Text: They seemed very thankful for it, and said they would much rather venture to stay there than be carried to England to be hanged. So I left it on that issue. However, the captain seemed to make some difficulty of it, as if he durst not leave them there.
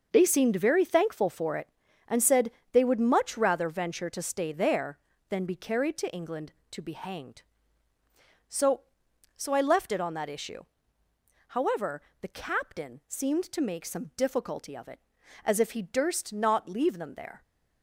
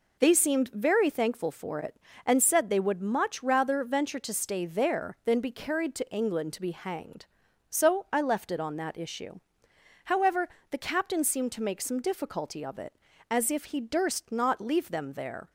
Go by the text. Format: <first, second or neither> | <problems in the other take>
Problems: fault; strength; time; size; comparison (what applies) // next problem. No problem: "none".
second | pauses between "said" and "they"; slight; at 2.5 s; 0.20 s long // says "So" twice; at 9.3 s